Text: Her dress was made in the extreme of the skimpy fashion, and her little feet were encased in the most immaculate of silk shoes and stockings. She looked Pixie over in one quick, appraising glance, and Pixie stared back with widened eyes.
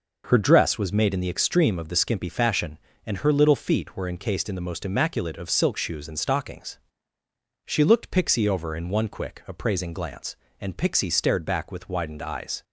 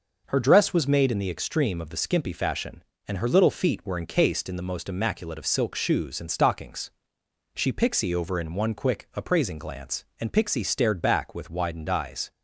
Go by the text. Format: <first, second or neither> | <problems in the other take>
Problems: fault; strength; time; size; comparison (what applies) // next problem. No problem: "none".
first | skips "looked"; at 7.7 s